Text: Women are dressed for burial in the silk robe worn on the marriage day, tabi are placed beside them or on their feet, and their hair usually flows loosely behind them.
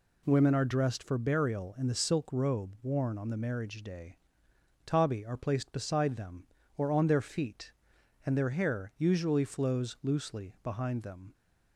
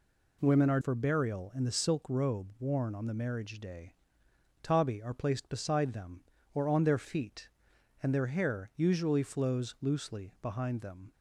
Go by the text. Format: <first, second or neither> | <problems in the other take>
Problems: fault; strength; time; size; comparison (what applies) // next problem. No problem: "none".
first | skips "dressed"; at 0.7 s